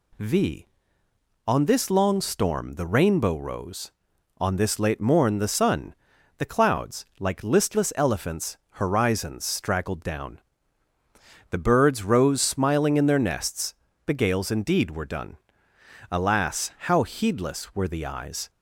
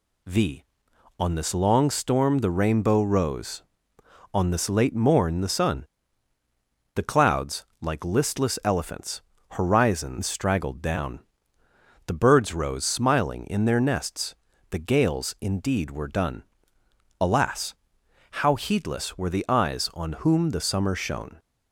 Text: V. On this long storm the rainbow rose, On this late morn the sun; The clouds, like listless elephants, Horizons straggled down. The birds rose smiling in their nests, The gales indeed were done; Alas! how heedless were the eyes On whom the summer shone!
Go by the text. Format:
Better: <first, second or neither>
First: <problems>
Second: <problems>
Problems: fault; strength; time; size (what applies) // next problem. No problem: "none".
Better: second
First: stops before "On whom the summer shone"; at 18.4 s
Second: none